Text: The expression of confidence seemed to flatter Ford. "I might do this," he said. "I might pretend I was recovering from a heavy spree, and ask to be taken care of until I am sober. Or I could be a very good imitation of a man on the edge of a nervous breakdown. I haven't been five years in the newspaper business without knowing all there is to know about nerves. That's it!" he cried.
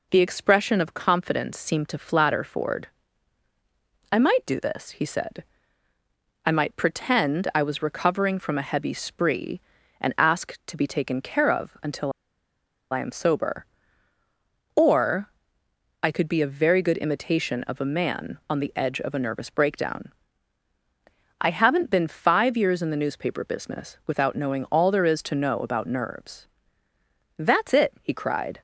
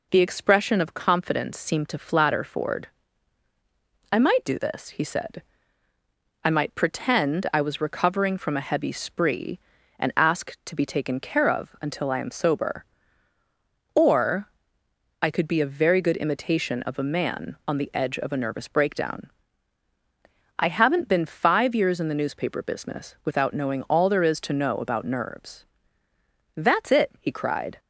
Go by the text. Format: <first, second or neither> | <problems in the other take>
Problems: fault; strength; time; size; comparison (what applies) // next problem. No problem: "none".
second | pauses between "until" and "I"; noticeable; at 12.1 s; 0.79 s long // pauses between "Or" and "I"; noticeable; at 15.2 s; 0.72 s long; noticeable in the second